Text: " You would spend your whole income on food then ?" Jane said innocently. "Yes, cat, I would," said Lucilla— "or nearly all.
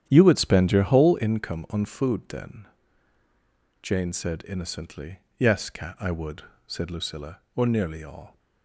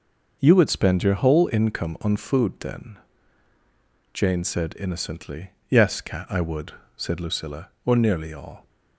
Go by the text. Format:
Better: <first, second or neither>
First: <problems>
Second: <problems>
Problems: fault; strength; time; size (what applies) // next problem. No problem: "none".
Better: second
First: starts louder than the rest; strong; until 1.3 s; 10 dB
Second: none